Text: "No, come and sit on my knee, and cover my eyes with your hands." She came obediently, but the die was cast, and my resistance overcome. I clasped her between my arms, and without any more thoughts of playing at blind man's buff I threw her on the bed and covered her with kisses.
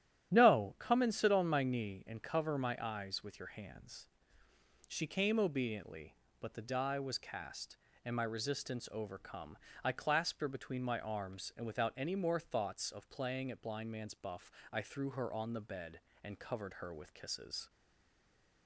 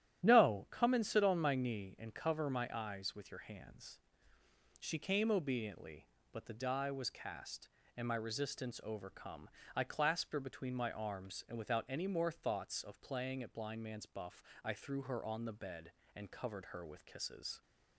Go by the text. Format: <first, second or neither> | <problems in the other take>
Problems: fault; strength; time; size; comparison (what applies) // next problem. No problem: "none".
second | starts louder than the rest; strong; until 1.3 s; 11.5 dB; strong in the second // pauses between "buff" and "I"; slight; at 14.4 s; 0.22 s long; slight in the second // stays silent after the last word; from 17.6 s on; 1.0 s long